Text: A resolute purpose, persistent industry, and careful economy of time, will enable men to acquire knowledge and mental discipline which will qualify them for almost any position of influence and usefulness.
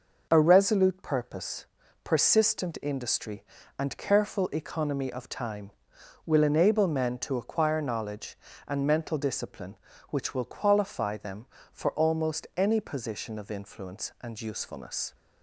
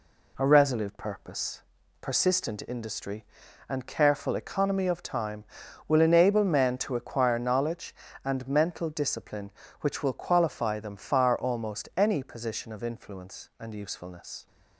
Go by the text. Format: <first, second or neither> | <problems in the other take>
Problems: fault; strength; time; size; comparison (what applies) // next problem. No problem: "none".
first | says "far" for "for"; at 10.9 s